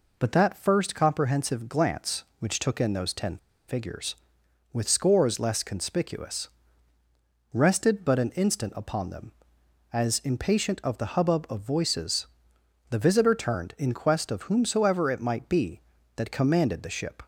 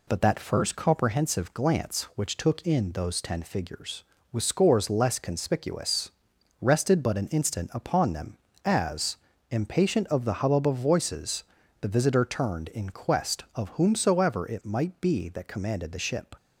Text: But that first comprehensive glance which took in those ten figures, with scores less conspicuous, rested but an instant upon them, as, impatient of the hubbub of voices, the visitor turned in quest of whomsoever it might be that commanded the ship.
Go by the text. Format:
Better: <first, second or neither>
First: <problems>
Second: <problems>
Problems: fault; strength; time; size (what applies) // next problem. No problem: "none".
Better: second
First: pauses between "ten" and "figures"; slight; at 3.3 s; 0.30 s long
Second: none